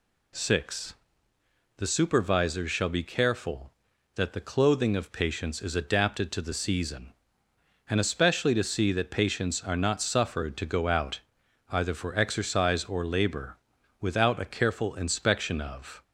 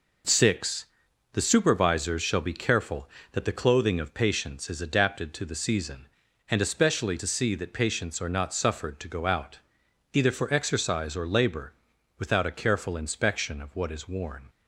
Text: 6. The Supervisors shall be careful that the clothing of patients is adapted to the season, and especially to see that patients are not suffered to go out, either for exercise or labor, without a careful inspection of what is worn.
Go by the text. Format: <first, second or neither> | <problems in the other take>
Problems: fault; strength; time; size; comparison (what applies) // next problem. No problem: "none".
second | stops before "what is worn"; at 16.0 s